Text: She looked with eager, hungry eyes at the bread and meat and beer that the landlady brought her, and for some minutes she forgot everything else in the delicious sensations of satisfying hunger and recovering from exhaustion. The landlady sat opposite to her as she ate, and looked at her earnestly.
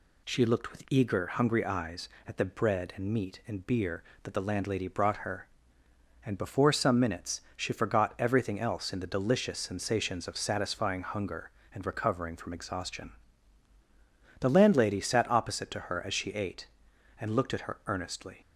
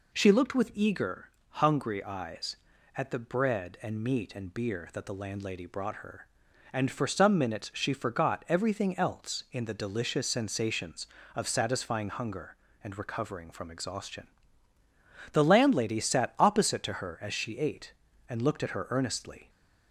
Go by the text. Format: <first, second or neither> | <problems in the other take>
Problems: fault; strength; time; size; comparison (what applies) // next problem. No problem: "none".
second | says "before" for "for"; at 6.3 s